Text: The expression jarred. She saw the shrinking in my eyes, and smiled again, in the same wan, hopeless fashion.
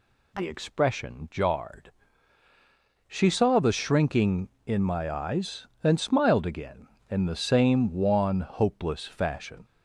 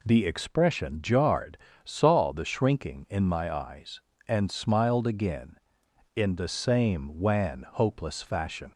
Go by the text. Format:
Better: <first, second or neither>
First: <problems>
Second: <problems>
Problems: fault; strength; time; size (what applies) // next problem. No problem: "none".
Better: first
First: none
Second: skips "She"; at 1.7 s